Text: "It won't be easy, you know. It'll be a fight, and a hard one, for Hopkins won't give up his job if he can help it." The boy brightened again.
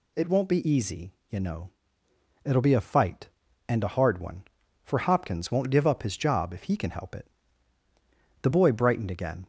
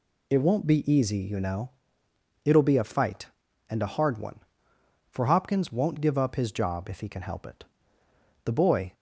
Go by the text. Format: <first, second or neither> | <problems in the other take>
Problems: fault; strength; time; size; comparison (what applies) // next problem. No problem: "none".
first | stops before "brightened again"; at 8.9 s